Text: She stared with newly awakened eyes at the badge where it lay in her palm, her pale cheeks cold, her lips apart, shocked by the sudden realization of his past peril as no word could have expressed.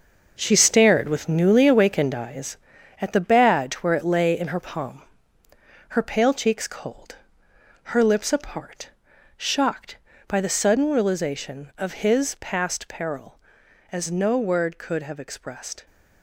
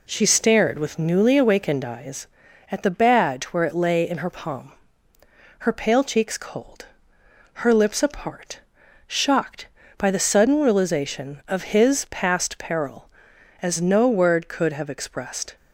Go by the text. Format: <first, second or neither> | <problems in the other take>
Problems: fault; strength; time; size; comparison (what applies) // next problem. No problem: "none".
second | gets quieter; strong; throughout; 10.5 dB